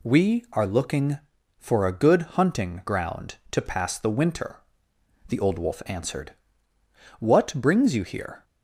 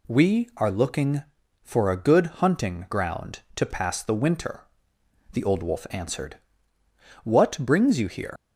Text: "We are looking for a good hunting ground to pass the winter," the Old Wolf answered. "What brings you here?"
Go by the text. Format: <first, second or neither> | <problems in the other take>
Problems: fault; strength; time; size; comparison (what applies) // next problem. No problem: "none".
first | leaves "here" unfinished; at 8.3 s; 120 ms